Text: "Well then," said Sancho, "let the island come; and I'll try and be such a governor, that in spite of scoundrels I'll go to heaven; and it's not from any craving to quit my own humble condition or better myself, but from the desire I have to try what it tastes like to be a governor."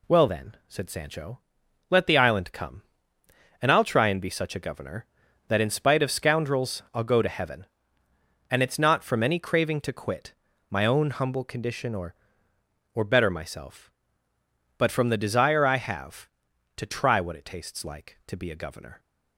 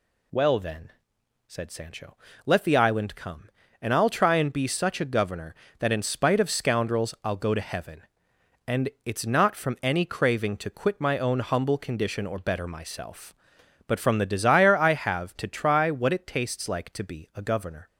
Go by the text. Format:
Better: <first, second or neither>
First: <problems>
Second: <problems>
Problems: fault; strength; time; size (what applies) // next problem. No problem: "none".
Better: second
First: pauses between "quit" and "my"; slight; at 10.3 s; 0.36 s long // says "or" twice; at 12.9 s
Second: none